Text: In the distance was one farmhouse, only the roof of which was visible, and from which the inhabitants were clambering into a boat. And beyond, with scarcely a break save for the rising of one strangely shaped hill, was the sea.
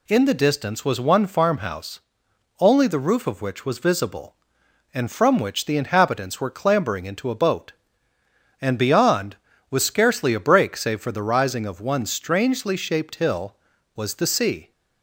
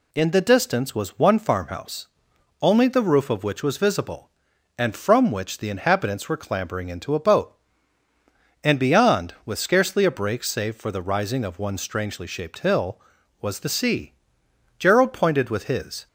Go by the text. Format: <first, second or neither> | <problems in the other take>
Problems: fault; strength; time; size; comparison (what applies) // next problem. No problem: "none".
first | goes on to say "Gerald pointed with his"; noticeable; from 14.7 s on; 1.2 s long